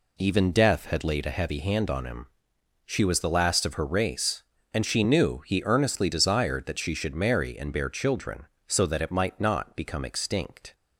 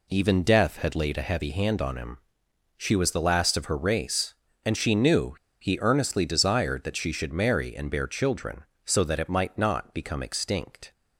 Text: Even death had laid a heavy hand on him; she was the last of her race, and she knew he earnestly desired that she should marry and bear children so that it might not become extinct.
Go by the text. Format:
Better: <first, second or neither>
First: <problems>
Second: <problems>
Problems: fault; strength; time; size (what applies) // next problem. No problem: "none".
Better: first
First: none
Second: pauses between "knew" and "he"; slight; at 5.3 s; 0.25 s long